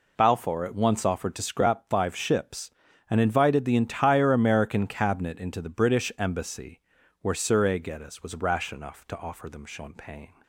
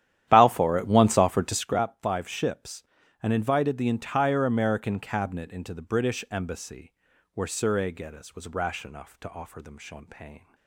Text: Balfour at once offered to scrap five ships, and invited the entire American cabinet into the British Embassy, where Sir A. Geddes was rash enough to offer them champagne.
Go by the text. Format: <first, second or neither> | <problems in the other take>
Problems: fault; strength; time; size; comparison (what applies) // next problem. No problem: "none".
first | starts louder than the rest; strong; until 1.7 s; 11.5 dB